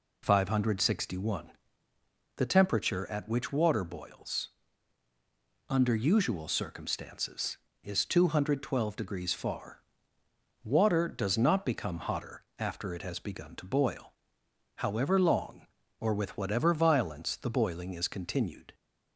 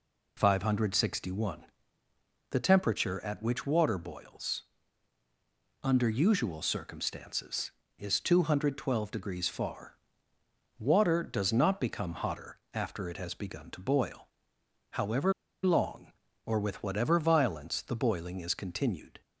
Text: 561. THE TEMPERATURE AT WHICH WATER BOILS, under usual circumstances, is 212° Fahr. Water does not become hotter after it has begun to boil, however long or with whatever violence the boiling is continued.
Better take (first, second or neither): first